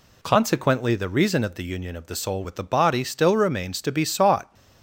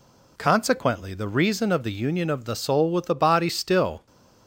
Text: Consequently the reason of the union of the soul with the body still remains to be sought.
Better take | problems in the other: first | stops before "remains to be sought"; at 4.0 s

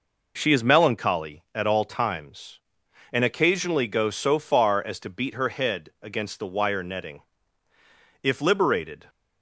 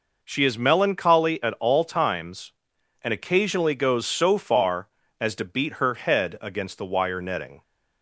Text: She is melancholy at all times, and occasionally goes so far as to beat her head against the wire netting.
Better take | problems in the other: second | goes on to say "If liberated"; noticeable; from 8.2 s on; 0.84 s long

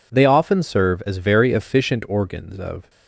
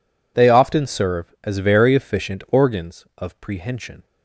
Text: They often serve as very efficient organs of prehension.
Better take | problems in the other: second | stops before "prehension"; at 2.8 s

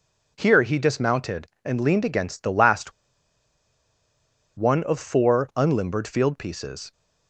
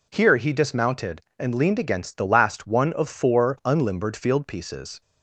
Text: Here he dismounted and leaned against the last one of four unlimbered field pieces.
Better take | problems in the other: second | pauses between "last" and "one"; strong; at 2.9 s; 1.6 s long

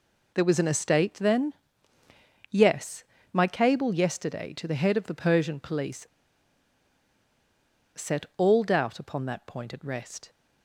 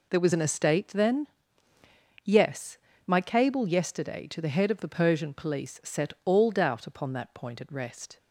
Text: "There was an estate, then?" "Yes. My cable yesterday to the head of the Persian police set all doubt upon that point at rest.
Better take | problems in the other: second | pauses between "police" and "set"; strong; at 6.0 s; 1.9 s long

